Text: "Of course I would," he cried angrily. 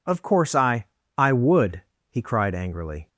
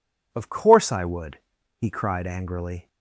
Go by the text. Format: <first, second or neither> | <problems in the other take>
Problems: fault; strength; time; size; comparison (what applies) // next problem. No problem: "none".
second | says "I" twice; at 1.1 s